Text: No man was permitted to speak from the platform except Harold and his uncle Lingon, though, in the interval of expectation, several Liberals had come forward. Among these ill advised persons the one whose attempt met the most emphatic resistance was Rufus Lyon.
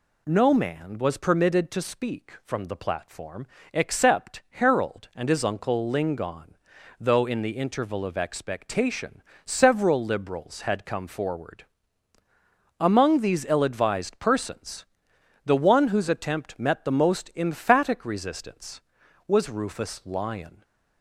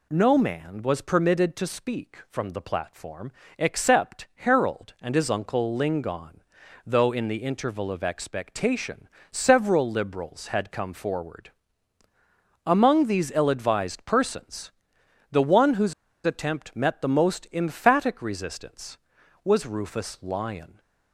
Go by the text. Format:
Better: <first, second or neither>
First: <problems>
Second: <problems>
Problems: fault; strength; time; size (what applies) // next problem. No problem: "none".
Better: first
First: pauses between "platform" and "except"; slight; at 3.4 s; 0.26 s long // pauses between "persons" and "the"; noticeable; at 14.8 s; 0.60 s long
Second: pauses between "platform" and "except"; slight; at 3.3 s; 0.26 s long // pauses between "persons" and "the"; noticeable; at 14.7 s; 0.60 s long // pauses between "whose" and "attempt"; slight; at 15.9 s; 0.33 s long